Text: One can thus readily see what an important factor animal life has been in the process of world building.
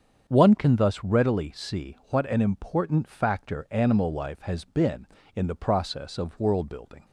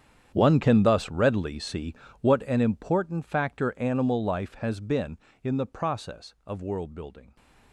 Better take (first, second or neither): first